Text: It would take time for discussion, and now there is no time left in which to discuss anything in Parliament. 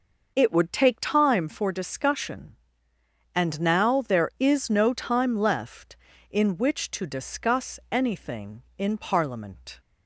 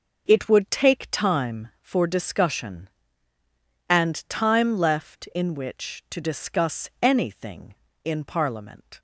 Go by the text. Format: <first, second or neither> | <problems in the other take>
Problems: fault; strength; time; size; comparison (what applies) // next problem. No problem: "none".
first | skips "now there is no"; at 4.2 s